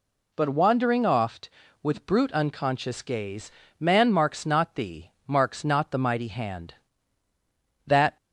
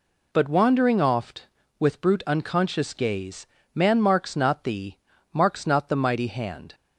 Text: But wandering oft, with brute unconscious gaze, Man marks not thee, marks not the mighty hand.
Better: second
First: goes on to say "That"; slight; from 7.8 s on; 0.30 s long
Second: none

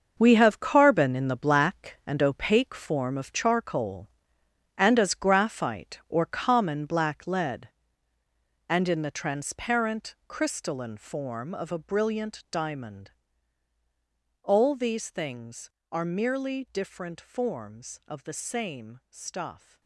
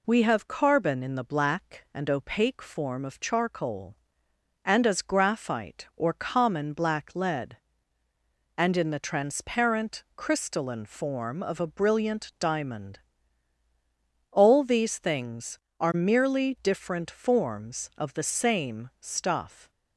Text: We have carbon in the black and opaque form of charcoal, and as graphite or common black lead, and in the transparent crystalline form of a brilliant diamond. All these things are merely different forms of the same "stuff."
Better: second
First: gets quieter; strong; throughout; 11 dB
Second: none

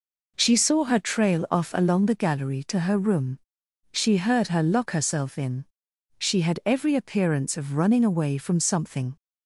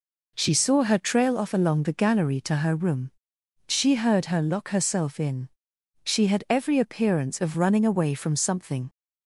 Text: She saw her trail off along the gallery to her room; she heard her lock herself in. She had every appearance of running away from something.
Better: neither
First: none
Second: none

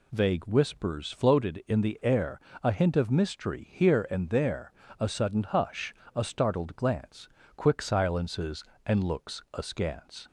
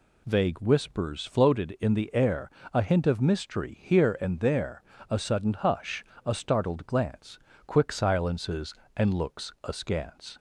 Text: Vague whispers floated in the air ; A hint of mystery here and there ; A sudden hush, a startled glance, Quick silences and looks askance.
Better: neither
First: none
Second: none

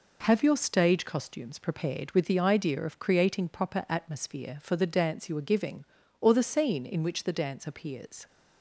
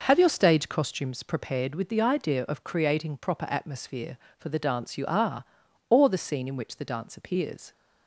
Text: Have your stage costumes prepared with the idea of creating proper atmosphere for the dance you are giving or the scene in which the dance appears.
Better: first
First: none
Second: skips "giving"; at 5.6 s

